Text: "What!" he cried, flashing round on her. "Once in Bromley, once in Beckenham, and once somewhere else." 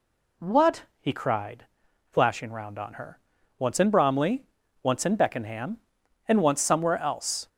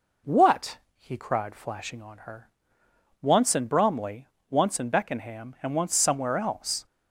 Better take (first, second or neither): first